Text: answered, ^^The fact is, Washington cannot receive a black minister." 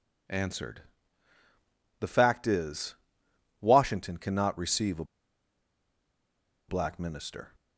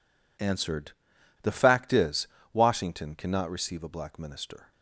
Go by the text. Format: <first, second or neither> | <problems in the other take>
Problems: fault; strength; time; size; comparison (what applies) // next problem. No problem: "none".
second | pauses between "a" and "black"; strong; at 5.0 s; 1.6 s long